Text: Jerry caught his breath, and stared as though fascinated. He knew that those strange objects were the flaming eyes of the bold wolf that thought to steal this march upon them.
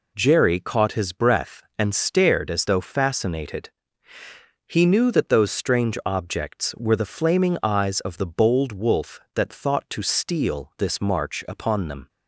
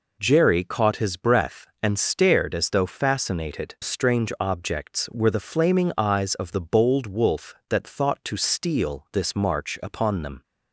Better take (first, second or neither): first